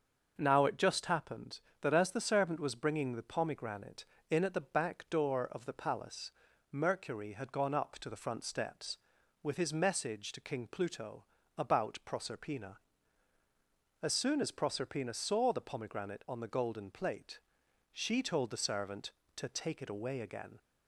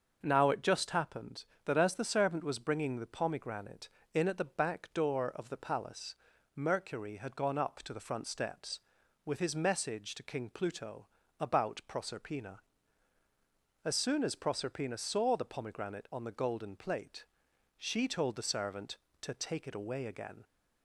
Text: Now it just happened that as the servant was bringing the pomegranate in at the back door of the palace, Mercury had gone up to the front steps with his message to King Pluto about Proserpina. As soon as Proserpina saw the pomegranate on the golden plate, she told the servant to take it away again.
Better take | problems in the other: neither | starts louder than the rest; the same in both // pauses between "Pluto" and "about"; slight; the same in both

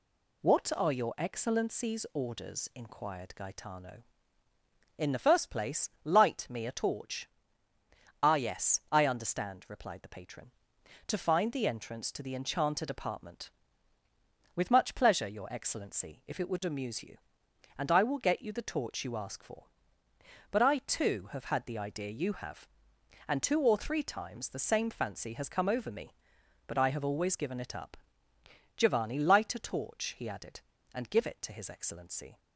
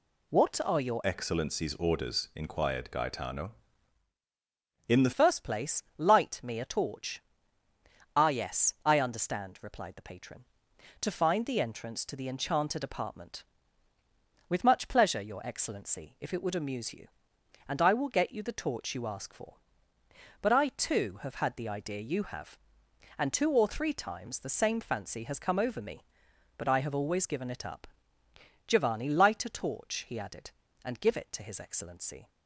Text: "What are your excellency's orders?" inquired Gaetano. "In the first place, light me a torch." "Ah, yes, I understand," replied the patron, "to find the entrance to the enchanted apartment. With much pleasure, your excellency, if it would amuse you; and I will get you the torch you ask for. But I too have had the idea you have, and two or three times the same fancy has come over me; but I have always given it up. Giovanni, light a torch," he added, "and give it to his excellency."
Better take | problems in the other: first | changes voice from "excellency's" to "the"; from 1.0 to 5.1 s; 4.1 s long

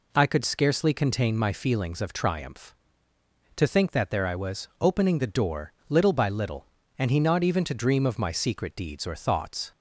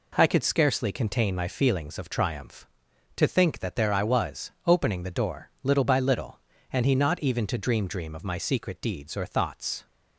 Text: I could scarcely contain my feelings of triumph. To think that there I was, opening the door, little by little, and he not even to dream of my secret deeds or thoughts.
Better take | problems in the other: first | says "dream" twice; at 7.8 s

